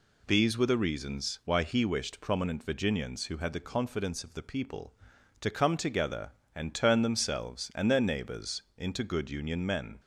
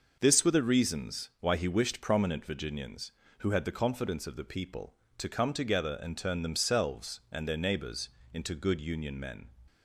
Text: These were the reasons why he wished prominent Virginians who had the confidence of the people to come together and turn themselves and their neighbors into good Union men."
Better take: first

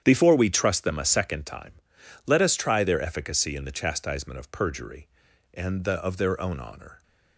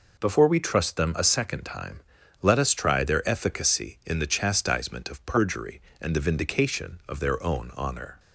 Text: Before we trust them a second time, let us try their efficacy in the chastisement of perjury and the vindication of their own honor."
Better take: second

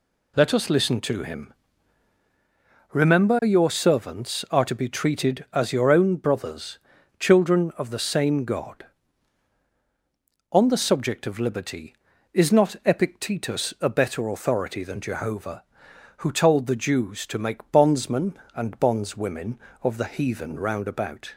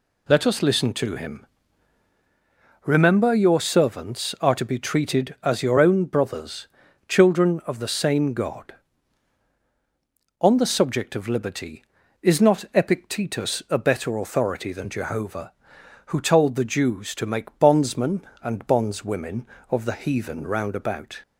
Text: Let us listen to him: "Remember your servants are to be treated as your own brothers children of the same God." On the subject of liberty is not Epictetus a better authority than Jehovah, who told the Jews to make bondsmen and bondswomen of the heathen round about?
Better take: neither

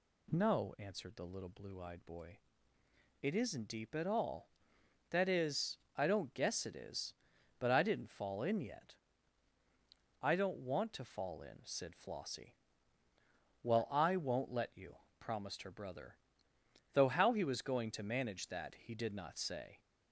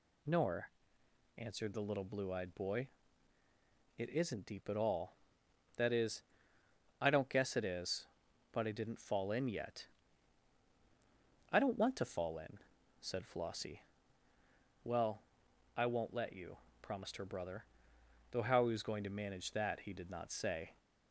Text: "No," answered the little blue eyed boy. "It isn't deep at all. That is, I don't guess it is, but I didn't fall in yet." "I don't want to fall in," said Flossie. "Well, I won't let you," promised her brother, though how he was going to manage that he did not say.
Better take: first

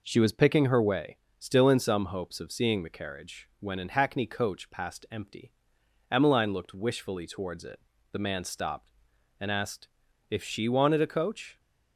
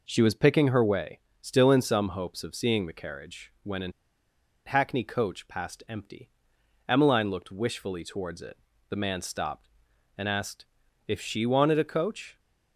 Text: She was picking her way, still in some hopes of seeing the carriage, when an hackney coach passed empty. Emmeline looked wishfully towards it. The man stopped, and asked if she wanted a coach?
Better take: first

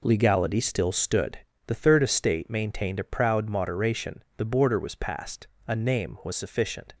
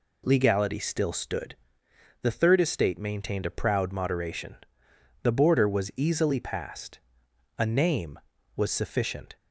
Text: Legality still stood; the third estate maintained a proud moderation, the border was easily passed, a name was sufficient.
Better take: second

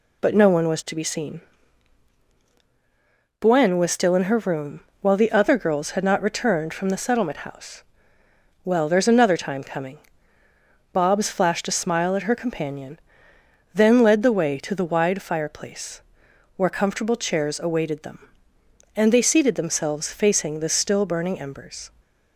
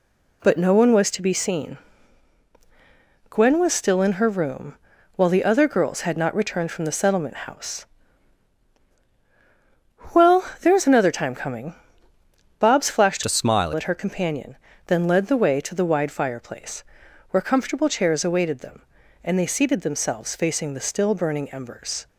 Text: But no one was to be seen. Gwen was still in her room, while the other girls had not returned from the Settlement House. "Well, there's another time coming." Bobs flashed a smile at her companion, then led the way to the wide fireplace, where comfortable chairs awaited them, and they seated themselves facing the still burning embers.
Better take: first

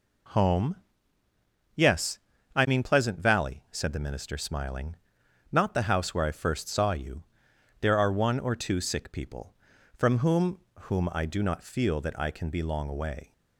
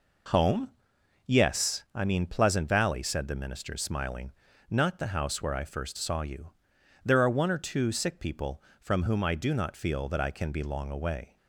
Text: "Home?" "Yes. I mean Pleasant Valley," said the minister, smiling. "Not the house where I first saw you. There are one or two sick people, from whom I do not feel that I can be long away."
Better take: second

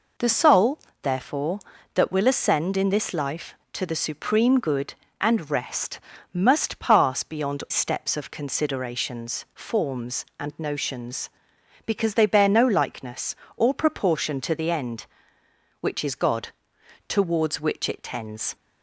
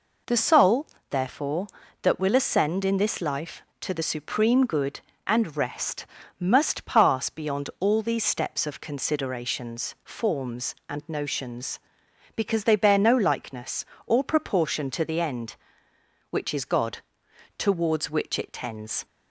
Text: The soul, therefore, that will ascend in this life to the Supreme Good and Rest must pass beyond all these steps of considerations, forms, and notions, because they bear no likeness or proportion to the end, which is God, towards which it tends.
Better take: second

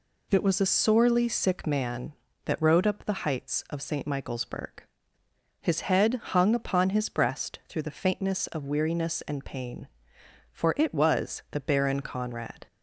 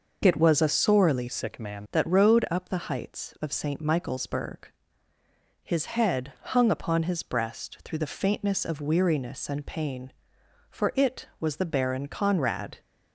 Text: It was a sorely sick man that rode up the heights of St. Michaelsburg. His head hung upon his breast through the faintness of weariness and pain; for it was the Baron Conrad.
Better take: first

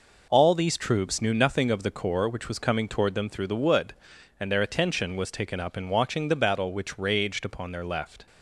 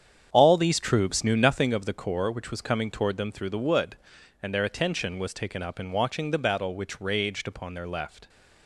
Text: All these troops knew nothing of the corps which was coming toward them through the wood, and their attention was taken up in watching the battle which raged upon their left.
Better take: first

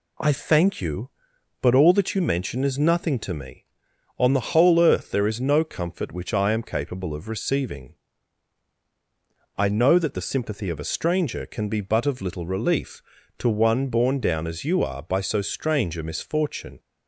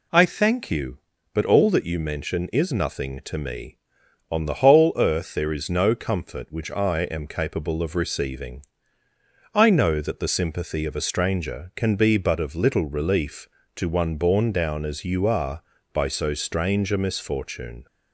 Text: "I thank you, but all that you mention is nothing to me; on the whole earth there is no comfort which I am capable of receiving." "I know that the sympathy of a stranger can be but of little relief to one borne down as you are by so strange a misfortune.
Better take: neither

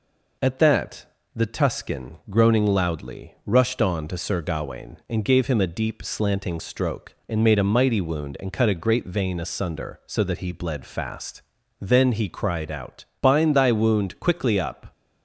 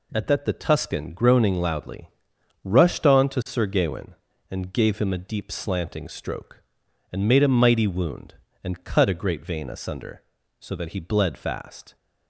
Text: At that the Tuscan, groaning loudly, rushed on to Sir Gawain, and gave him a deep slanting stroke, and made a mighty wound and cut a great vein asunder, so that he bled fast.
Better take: second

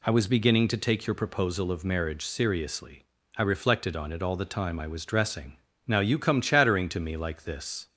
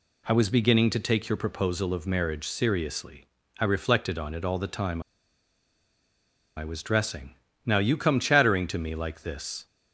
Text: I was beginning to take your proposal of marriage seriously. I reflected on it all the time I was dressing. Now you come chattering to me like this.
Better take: first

